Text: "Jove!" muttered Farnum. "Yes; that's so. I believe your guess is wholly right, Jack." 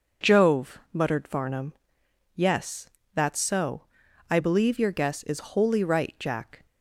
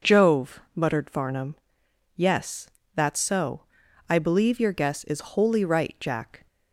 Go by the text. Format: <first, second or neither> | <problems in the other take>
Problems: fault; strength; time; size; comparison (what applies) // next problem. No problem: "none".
neither | none